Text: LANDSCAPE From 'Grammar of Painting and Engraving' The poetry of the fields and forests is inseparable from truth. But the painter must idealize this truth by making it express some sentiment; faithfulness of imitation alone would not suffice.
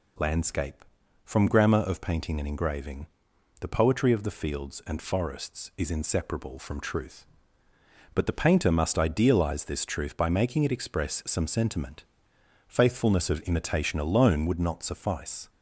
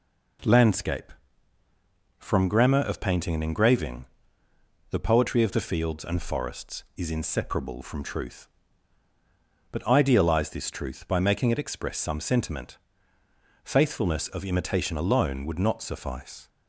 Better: first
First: pauses between "Engraving" and "The"; noticeable; at 3.0 s; 0.54 s long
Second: pauses between "Engraving" and "The"; noticeable; at 4.0 s; 0.82 s long // skips "the painter must"; at 9.8 s

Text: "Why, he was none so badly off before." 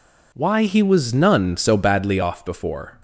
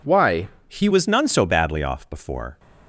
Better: first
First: none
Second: changes voice at "was"; from 0.9 s on; 1.6 s long

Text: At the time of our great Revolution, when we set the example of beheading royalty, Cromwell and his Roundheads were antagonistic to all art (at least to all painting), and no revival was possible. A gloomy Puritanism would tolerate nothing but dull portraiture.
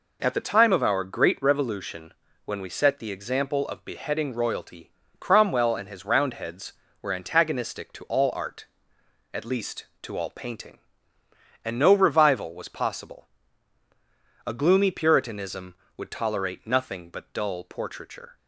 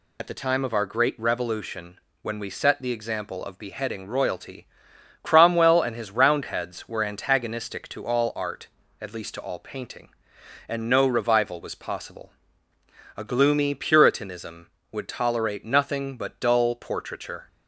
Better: first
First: none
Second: loses the start of "At"; at 0.1 s; 45 ms

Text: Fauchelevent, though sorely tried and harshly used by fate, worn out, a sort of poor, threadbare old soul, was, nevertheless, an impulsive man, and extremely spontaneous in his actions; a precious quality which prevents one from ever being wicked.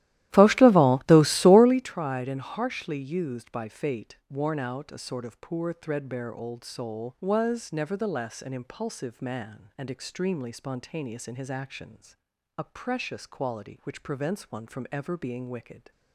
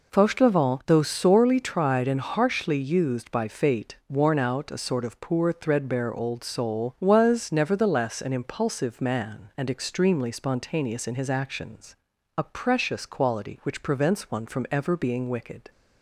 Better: second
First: starts louder than the rest; strong; until 1.8 s; 14.5 dB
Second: none

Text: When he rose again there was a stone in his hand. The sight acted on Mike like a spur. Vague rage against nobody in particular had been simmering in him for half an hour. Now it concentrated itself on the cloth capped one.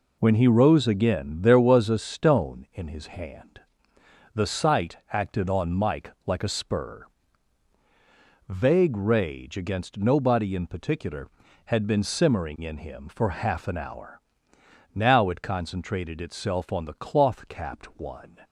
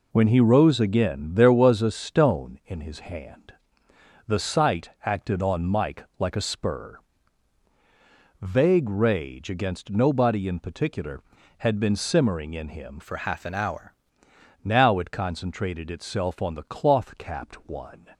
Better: first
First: pauses between "sight" and "acted"; slight; at 4.9 s; 0.16 s long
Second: pauses between "sight" and "acted"; slight; at 4.8 s; 0.16 s long // changes voice from "for" to "hour"; from 13.0 to 13.9 s; 0.9 s long

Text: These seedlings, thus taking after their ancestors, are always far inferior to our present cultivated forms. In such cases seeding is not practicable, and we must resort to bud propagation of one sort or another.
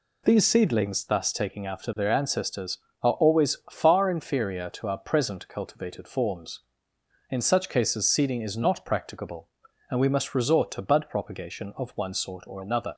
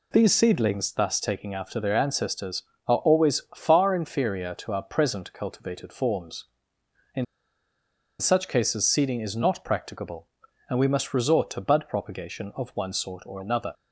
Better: first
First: none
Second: pauses between "In" and "such"; noticeable; at 7.2 s; 0.94 s long

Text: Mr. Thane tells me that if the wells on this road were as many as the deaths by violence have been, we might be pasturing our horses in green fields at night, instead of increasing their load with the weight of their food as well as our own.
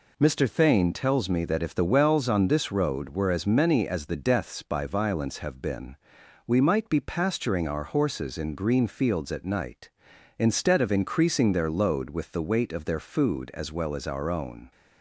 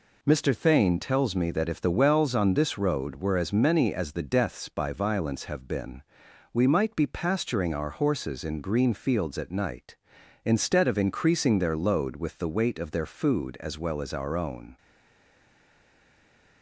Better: first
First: none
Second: stays silent after the last word; noticeable; from 14.7 s on; 1.9 s long

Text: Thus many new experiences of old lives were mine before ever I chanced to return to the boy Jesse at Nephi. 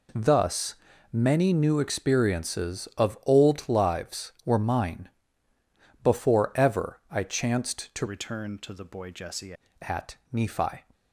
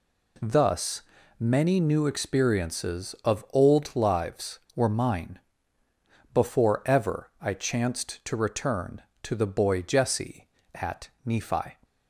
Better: second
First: pauses between "Thus" and "many"; at 0.7 s; 0.38 s long // pauses between "mine" and "before"; noticeable; at 5.0 s; 0.94 s long // changes voice from "return" to "Jesse"; from 8.0 to 9.5 s; 1.5 s long // pauses between "at" and "Nephi"; slight; at 10.1 s; 0.16 s long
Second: pauses between "Thus" and "many"; at 1.0 s; 0.38 s long // pauses between "mine" and "before"; noticeable; at 5.3 s; 0.94 s long // pauses between "at" and "Nephi"; slight; at 11.0 s; 0.16 s long

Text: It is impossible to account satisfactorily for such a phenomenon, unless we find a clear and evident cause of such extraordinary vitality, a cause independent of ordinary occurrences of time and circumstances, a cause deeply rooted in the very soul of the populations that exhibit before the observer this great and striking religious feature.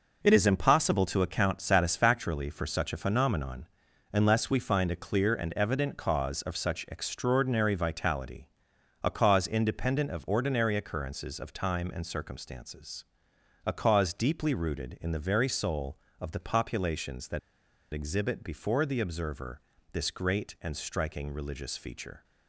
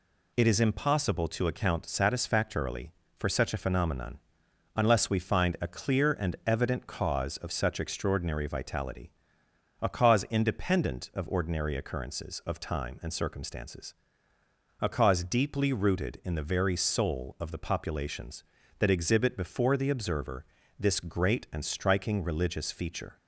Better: second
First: pauses between "that" and "exhibit"; noticeable; at 17.3 s; 0.53 s long // pauses between "observer" and "this"; slight; at 19.6 s; 0.30 s long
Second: pauses between "observer" and "this"; slight; at 20.4 s; 0.34 s long

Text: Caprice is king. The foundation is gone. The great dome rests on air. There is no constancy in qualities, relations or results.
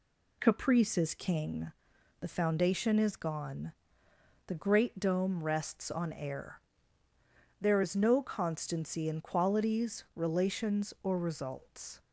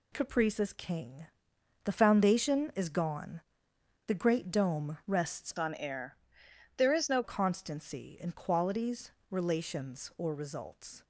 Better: first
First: none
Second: changes voice from "on" to "no"; from 5.5 to 7.2 s; 1.7 s long

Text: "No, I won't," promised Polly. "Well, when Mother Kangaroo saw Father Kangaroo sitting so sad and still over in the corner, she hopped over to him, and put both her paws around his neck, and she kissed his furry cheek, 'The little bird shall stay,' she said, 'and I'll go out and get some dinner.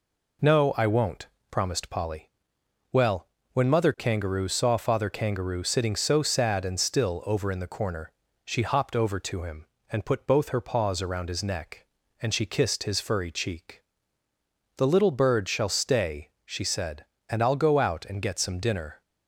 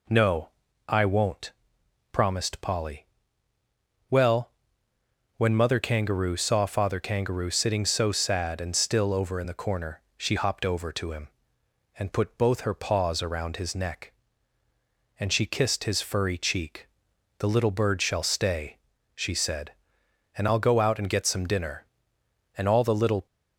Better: first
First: none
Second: goes on to say "And all the little"; noticeable; from 22.5 s on; 0.68 s long

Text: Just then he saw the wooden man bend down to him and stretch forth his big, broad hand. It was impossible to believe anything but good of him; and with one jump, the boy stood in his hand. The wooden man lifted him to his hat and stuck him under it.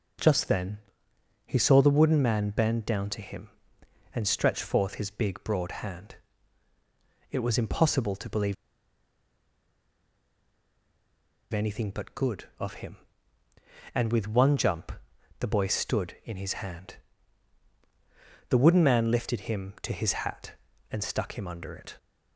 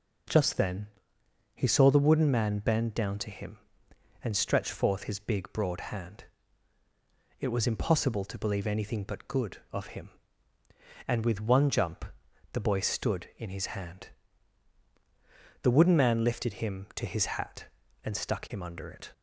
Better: second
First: pauses between "then" and "he"; noticeable; at 0.7 s; 0.66 s long // pauses between "believe" and "anything"; strong; at 8.5 s; 2.9 s long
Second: pauses between "then" and "he"; noticeable; at 0.8 s; 0.66 s long

